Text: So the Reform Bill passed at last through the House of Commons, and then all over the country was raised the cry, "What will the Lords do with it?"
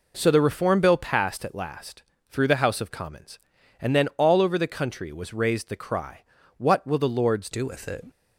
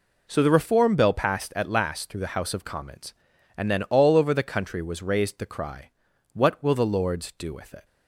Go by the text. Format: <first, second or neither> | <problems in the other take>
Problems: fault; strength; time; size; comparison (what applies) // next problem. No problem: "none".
second | pauses between "last" and "through"; slight; at 2.0 s; 0.28 s long // changes voice at "do"; from 7.5 s on; 0.5 s long